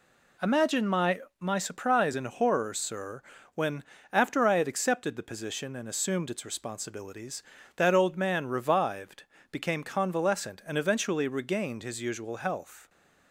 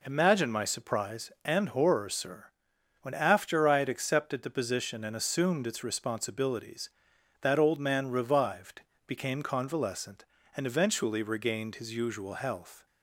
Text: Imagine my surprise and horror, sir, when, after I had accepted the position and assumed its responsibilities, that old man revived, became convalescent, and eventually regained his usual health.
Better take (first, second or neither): second